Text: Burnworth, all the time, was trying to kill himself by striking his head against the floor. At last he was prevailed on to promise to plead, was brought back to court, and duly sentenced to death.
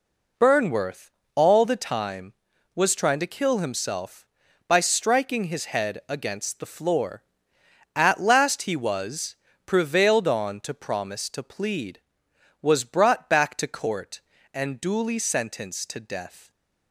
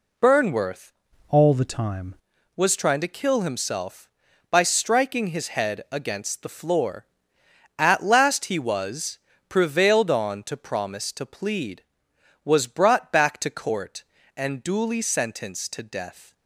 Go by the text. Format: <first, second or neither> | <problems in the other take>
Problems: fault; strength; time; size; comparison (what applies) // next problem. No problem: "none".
first | changes voice from "all" to "time"; from 1.2 to 2.1 s; 0.9 s long // pauses between "was" and "prevailed"; slight; at 9.1 s; 0.32 s long; slight in the first